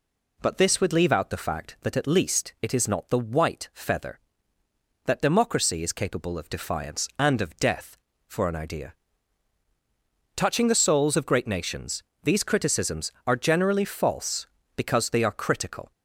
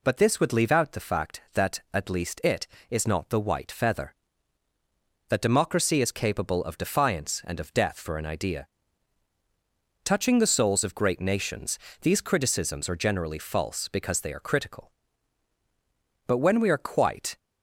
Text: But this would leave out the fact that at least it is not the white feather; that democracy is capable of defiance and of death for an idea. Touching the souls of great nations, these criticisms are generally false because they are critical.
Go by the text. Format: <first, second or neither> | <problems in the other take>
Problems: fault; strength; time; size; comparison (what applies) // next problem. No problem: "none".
first | goes on to say "But when we are quite"; noticeable; from 16.2 s on; 1.1 s long